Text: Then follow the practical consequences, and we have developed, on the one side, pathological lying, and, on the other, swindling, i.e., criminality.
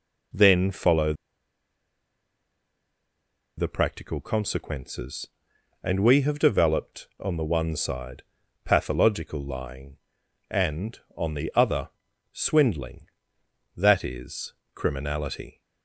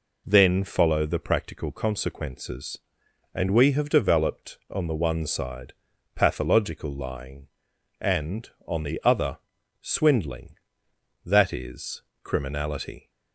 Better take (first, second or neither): second